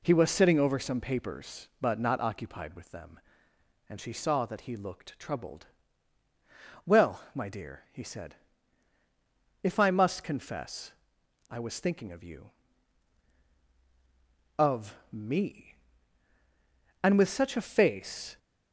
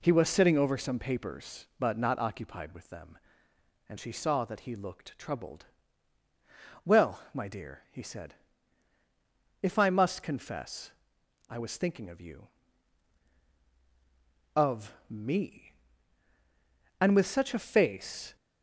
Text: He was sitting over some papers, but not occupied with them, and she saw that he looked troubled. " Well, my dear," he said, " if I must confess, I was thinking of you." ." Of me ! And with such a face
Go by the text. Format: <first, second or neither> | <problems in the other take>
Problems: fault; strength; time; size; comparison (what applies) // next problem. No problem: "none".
neither | pauses between "Of" and "me"; slight; the same in both